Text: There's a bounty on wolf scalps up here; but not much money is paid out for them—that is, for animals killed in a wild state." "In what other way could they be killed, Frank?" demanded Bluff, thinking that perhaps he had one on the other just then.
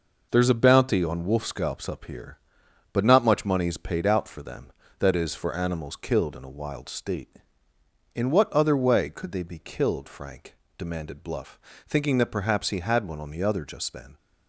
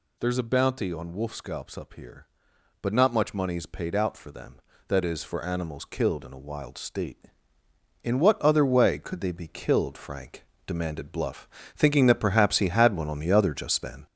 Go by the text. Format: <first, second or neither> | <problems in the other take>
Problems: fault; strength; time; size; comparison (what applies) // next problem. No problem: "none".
first | gets louder; noticeable; throughout; 4.5 dB